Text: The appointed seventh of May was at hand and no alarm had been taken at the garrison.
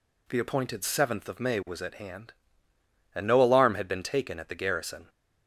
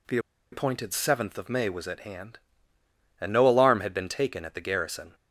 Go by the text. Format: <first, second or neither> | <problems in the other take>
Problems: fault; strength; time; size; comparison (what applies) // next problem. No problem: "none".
first | pauses between "The" and "appointed"; slight; at 0.1 s; 0.35 s long